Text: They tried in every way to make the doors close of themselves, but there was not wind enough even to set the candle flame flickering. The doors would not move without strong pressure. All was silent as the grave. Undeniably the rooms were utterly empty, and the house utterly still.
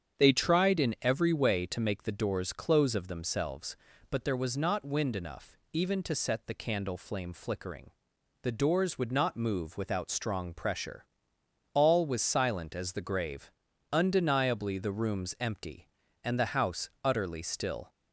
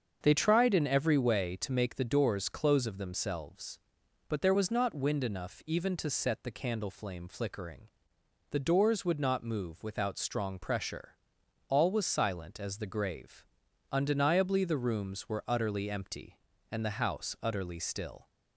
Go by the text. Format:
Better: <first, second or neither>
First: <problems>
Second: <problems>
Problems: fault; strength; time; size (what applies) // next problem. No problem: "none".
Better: second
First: starts louder than the rest; strong; until 1.2 s; 7.5 dB // skips "were utterly"; at 15.3 s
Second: starts louder than the rest; until 1.2 s; 6.5 dB